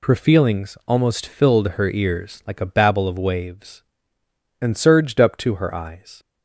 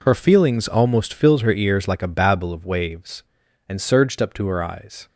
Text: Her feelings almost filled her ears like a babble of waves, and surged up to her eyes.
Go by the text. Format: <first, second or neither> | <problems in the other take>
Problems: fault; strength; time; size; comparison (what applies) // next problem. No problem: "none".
neither | none